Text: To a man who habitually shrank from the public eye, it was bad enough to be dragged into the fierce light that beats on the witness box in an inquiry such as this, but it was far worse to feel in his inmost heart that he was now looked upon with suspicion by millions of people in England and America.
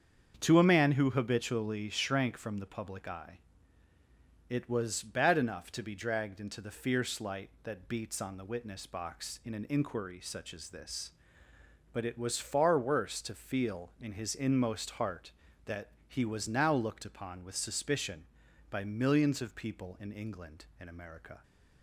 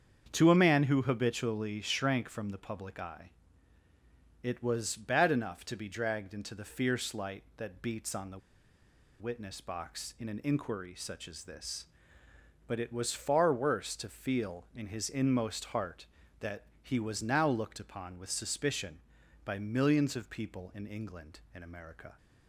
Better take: first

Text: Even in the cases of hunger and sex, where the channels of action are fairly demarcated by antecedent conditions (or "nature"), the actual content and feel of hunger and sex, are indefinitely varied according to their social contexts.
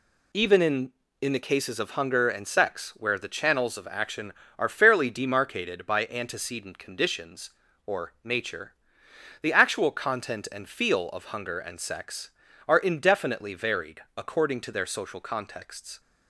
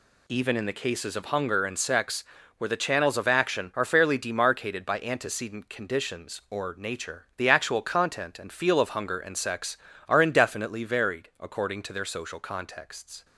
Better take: second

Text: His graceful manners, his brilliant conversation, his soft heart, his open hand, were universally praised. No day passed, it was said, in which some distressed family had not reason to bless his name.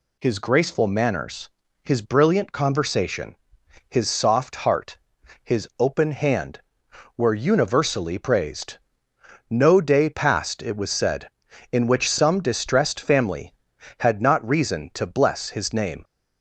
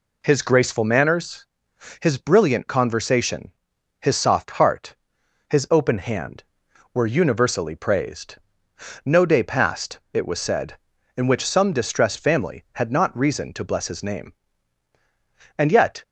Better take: first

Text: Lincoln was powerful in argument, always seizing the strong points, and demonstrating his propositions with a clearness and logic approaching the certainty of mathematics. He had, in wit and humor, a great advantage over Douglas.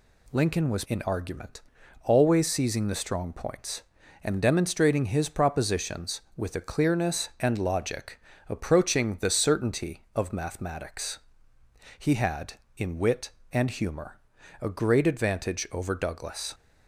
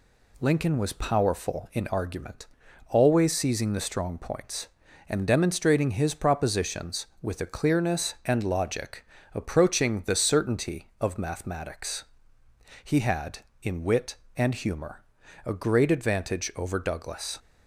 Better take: second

